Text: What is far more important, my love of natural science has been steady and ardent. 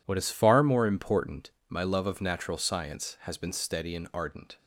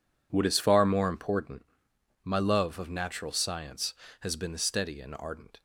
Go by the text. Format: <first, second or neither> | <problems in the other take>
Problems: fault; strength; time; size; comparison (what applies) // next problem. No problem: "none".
neither | none